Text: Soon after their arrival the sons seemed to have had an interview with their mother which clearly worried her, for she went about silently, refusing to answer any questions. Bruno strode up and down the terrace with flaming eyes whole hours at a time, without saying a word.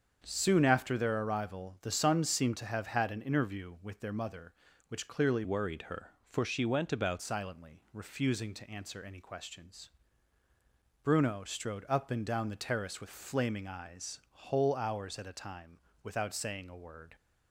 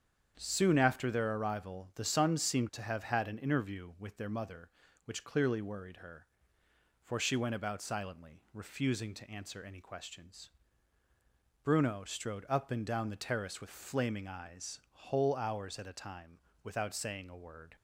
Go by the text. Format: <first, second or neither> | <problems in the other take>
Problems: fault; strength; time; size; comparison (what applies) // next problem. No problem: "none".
second | starts louder than the rest; strong; until 1.2 s; 7 dB; strong in the second // changes voice from "worried" to "about"; from 5.4 to 7.2 s; 1.8 s long